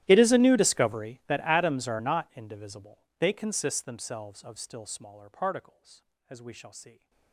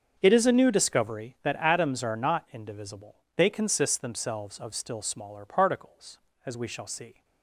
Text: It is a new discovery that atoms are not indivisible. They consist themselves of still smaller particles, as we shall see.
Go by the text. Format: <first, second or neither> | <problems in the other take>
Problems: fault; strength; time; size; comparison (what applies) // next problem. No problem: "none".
second | gets quieter; strong; throughout; 27.5 dB // starts louder than the rest; strong; until 1.0 s; 14 dB; strong in the second